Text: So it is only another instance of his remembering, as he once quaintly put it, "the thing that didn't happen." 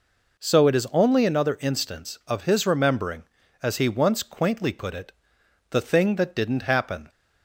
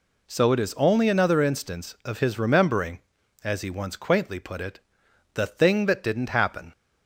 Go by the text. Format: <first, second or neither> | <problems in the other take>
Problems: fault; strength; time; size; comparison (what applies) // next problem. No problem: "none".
neither | none